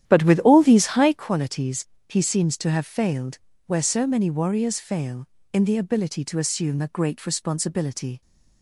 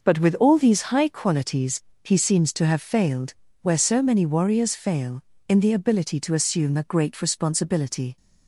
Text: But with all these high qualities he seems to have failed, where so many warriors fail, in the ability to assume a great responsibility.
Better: second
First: starts louder than the rest; strong; until 1.3 s; 10.5 dB // pauses between "qualities" and "he"; slight; at 1.8 s; 0.20 s long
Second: pauses between "qualities" and "he"; slight; at 1.8 s; 0.20 s long

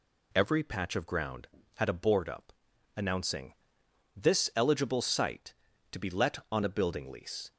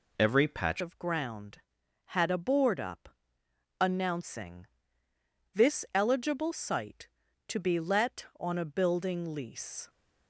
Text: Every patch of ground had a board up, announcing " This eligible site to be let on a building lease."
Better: first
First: none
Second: changes voice at "of"; from 0.8 s on; 9.0 s long

